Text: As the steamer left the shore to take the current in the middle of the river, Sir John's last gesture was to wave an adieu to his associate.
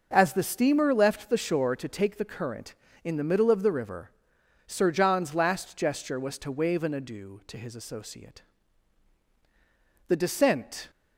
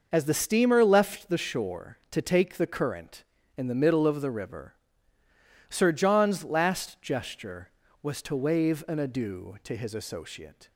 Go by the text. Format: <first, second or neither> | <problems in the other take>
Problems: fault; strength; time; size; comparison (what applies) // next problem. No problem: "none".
second | goes on to say "The descent"; noticeable; from 10.0 s on; 0.82 s long